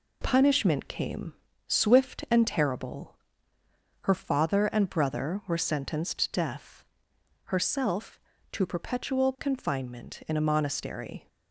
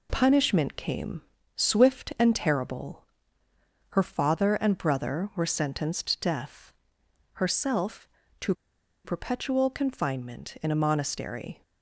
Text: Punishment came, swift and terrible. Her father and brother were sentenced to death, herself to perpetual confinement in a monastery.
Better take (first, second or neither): first